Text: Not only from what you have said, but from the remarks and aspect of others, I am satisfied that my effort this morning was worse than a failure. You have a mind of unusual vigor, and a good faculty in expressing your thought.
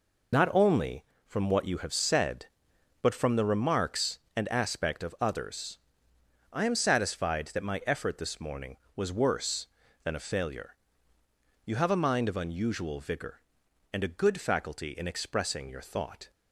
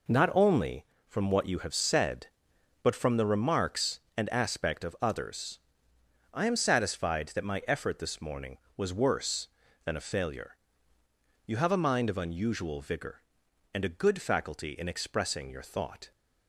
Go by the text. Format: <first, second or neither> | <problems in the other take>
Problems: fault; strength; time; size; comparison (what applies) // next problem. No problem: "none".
second | loses the start of "Not"; at 0.3 s; 55 ms